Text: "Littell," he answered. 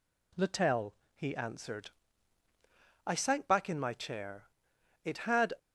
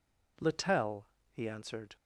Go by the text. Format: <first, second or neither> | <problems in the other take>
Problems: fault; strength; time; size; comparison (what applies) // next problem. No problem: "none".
second | goes on to say "I sank back in my chair it had"; strong; from 3.0 s on; 2.4 s long